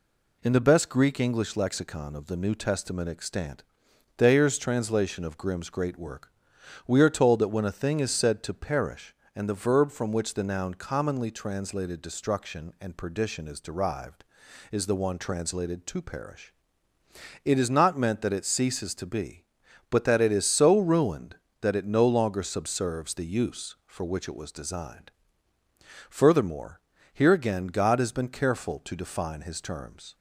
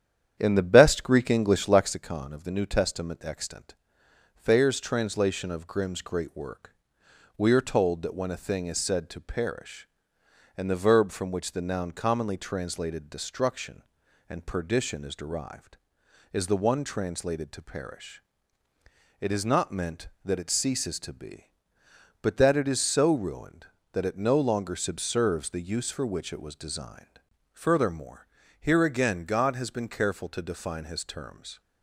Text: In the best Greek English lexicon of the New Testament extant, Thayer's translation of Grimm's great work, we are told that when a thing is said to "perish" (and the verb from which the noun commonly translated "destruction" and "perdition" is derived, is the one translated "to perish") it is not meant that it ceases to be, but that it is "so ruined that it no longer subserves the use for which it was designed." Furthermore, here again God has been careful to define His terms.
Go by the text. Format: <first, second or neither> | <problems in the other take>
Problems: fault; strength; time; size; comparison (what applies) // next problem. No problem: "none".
first | starts louder than the rest; strong; until 2.0 s; 9.5 dB